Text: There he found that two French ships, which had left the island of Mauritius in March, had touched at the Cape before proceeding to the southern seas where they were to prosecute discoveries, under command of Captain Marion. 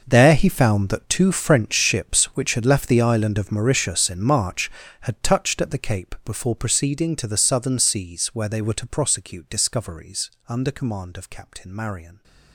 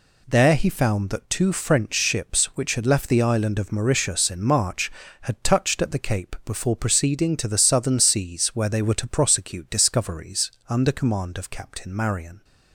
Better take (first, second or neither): second